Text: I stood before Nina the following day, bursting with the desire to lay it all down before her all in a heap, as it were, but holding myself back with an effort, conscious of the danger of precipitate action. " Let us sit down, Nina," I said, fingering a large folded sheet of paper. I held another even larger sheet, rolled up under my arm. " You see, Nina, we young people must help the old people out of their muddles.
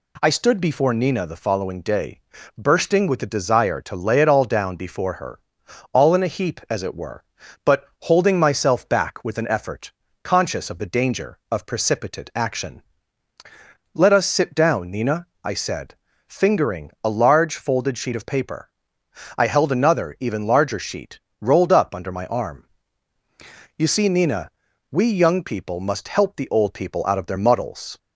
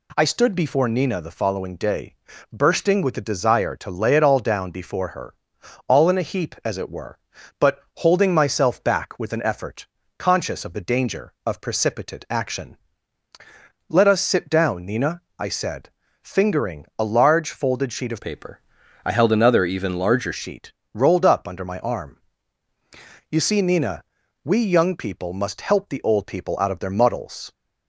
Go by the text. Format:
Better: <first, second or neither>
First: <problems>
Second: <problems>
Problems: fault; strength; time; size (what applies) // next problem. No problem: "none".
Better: first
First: pauses between "her" and "all"; noticeable; at 5.4 s; 0.52 s long // pauses between "but" and "holding"; slight; at 7.8 s; 0.16 s long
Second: pauses between "her" and "all"; noticeable; at 5.3 s; 0.52 s long // pauses between "but" and "holding"; slight; at 7.7 s; 0.16 s long // changes voice from "paper" to "larger"; from 18.2 to 20.3 s; 2.1 s long